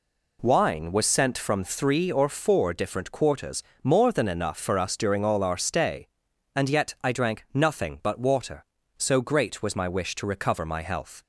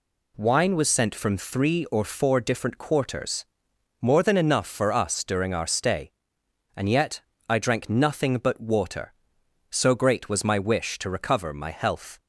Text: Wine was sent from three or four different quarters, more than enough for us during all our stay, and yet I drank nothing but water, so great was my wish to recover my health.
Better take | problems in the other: first | skips "all"; at 5.5 s // pauses between "yet" and "I"; slight; at 7.2 s; 0.26 s long

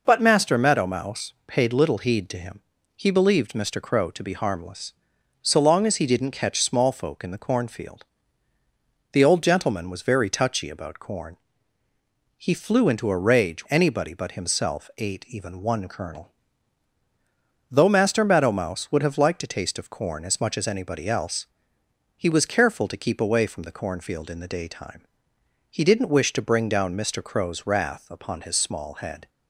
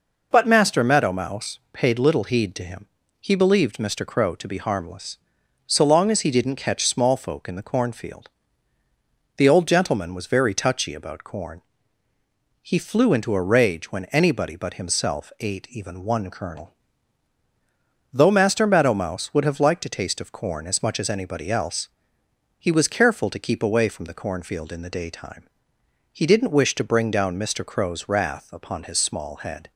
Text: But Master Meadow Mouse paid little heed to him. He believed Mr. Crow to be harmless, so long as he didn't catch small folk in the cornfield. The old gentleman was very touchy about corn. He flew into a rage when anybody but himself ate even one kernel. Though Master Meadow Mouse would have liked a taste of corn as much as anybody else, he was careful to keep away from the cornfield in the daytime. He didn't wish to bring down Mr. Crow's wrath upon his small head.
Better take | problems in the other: second | pauses between "Mouse" and "paid"; slight; at 1.3 s; 0.16 s long; slight in the second // skips "when"; at 13.6 s

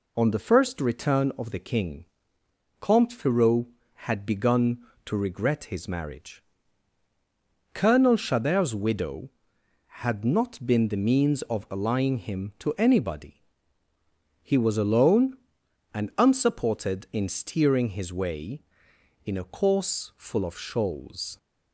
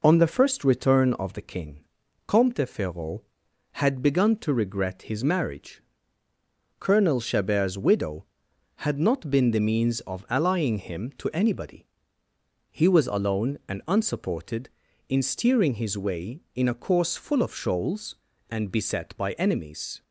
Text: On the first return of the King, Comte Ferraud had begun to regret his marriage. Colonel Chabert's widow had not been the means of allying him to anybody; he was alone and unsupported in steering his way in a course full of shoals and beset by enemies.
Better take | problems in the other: second | stops before "and beset by enemies"; at 21.3 s

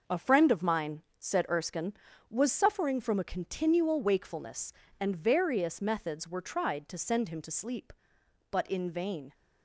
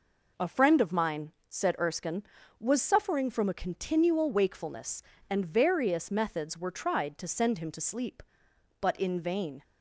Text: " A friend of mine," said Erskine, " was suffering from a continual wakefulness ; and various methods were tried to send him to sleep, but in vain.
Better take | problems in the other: second | gets quieter; noticeable; throughout; 5 dB

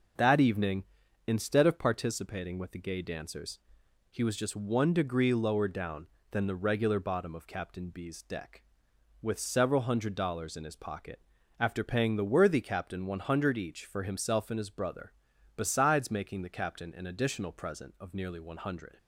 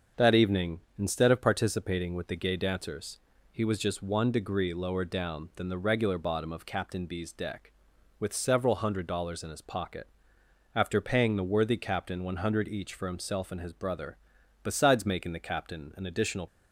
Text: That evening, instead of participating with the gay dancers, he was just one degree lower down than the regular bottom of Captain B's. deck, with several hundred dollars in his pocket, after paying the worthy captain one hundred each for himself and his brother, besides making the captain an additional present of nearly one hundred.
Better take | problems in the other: first | starts louder than the rest; until 1.3 s; 7 dB; noticeable in the first // stops before "present of nearly one hundred"; at 16.4 s

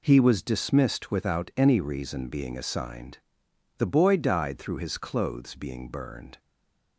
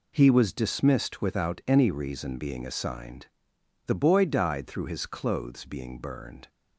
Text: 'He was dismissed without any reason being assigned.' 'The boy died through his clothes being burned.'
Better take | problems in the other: second | stays silent after the last word; slight; from 6.3 s on; 0.6 s long

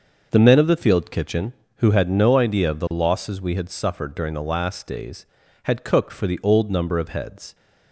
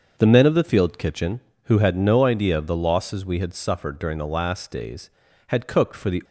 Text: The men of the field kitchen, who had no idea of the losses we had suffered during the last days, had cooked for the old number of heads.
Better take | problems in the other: first | starts louder than the rest; until 1.1 s; 6.5 dB; noticeable in the first // stops before "old number of heads"; at 6.2 s

